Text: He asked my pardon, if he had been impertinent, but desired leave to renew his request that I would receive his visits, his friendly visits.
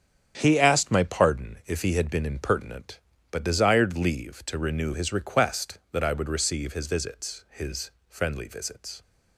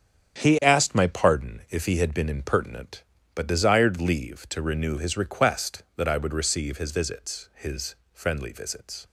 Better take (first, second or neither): neither